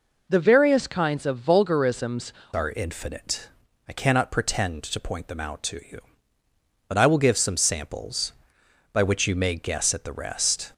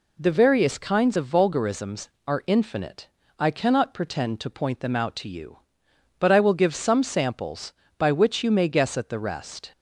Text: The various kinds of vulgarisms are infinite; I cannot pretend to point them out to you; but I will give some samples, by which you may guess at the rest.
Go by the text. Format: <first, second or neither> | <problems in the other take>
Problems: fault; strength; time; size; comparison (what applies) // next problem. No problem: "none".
second | changes voice at "are"; from 2.5 s on; 8.2 s long